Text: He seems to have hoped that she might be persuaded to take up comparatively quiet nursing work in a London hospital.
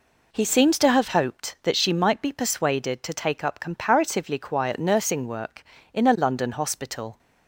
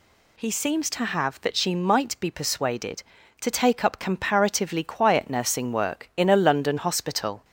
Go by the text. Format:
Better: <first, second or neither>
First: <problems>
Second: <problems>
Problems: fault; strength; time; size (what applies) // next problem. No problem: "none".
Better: first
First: none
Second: skips "hoped"; at 1.4 s